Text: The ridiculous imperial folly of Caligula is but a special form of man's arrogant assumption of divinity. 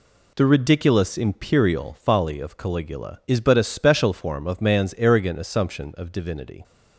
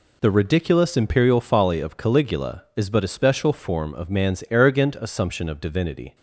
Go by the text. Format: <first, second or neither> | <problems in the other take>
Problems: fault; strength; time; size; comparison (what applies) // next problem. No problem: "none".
neither | none